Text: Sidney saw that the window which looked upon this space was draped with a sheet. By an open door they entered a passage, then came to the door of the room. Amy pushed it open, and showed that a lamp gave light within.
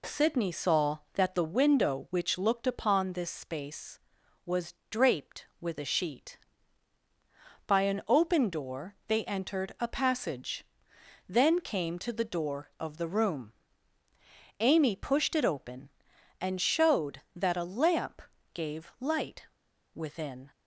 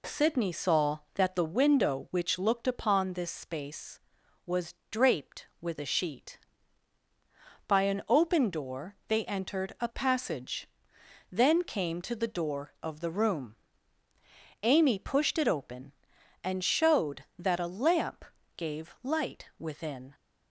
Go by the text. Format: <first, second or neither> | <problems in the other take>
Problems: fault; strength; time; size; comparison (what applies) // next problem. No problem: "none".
second | pauses between "was" and "draped"; slight; at 4.7 s; 0.16 s long; slight in the second // pauses between "lamp" and "gave"; slight; at 18.2 s; 0.32 s long; slight in the second // pauses between "light" and "within"; noticeable; at 19.4 s; 0.48 s long